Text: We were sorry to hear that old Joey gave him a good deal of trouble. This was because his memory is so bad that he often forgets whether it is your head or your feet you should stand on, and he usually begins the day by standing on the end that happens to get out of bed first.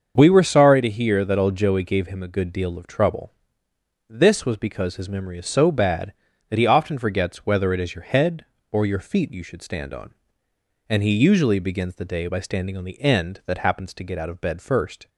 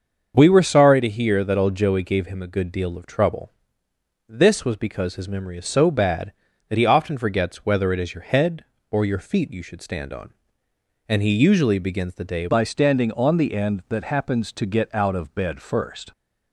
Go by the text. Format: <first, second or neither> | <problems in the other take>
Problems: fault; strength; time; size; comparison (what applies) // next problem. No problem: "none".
first | starts louder than the rest; until 1.3 s; 6.5 dB; also in the first // changes voice at "by"; from 12.4 s on; 3.7 s long